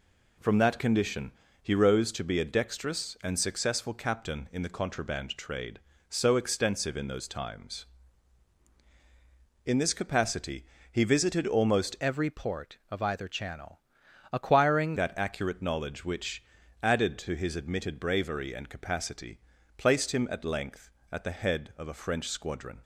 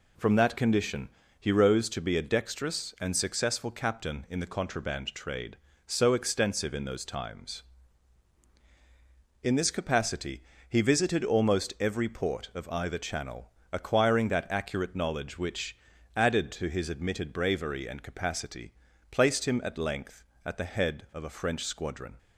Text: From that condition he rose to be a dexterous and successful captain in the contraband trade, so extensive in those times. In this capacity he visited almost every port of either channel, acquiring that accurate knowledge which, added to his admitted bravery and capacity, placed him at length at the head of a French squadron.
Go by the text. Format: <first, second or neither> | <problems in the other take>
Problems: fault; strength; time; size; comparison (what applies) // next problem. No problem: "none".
second | pauses between "condition" and "he"; slight; at 1.3 s; 0.28 s long; slight in the second // pauses between "capacity" and "he"; slight; at 10.6 s; 0.26 s long; slight in the second // changes voice from "every" to "acquiring"; from 12.0 to 14.9 s; 2.9 s long